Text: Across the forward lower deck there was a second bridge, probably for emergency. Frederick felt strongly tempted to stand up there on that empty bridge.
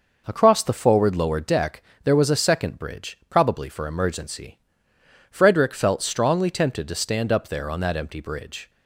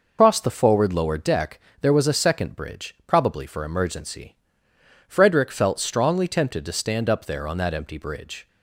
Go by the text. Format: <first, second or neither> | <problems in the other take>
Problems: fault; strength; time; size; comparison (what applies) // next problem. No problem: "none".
first | loses the start of "Across"; at 0.1 s; 155 ms // pauses between "deck" and "there"; slight; at 1.5 s; 0.22 s long; slight in the first